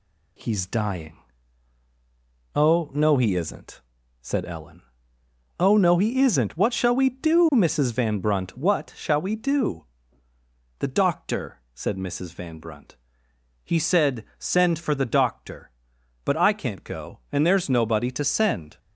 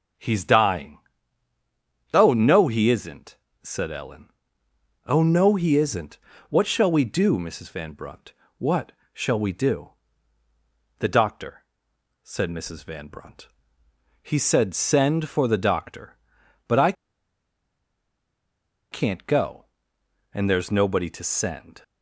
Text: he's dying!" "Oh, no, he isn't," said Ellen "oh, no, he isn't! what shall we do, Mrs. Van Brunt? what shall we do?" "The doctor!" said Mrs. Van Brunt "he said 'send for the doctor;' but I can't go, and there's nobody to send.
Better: first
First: pauses between "Ellen" and "oh"; noticeable; at 4.8 s; 0.76 s long // pauses between "Brunt" and "he"; noticeable; at 12.9 s; 0.70 s long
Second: starts louder than the rest; until 2.3 s; 6.5 dB // pauses between "Ellen" and "oh"; noticeable; at 4.2 s; 0.78 s long // pauses between "what" and "shall"; slight; at 8.9 s; 0.20 s long // pauses between "Brunt" and "he"; noticeable; at 13.4 s; 0.74 s long // pauses between "I" and "can't"; strong; at 16.9 s; 1.9 s long

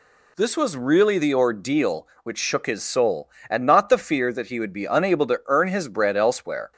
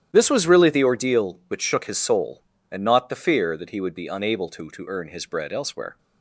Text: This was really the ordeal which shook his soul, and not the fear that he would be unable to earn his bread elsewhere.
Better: first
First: none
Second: starts louder than the rest; strong; until 1.1 s; 11 dB // says "to" twice; at 4.6 s

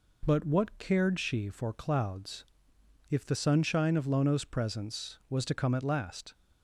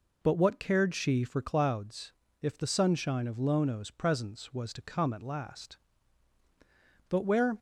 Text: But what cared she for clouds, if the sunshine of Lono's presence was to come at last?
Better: first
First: none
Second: goes on to say "But where"; slight; from 7.0 s on; 0.48 s long

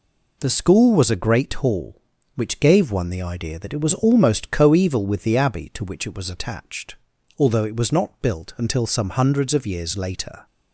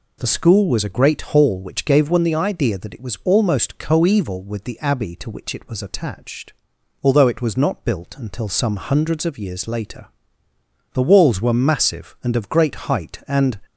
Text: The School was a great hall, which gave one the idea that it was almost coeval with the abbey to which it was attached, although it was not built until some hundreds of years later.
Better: first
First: none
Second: goes on to say "The walls were massive and of great height and"; strong; from 10.9 s on; 2.6 s long

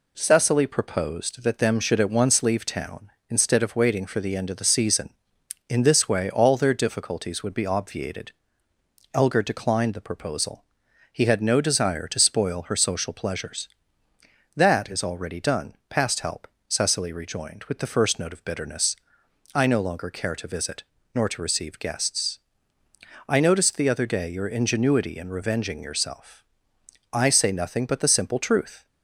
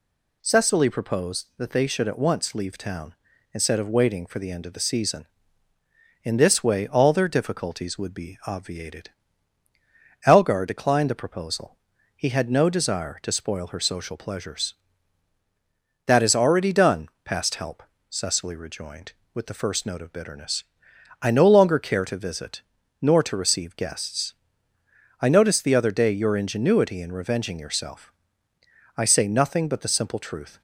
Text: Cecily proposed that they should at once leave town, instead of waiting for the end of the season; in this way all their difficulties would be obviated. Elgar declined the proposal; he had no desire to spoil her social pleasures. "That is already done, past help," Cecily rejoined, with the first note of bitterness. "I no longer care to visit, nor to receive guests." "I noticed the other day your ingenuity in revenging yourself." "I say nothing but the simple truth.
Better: second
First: says "them" for "they"; at 1.5 s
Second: none

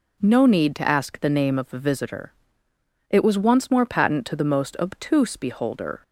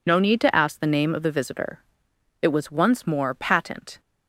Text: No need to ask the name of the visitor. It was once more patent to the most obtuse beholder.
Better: first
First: none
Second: stops before "to the most obtuse beholder"; at 3.9 s

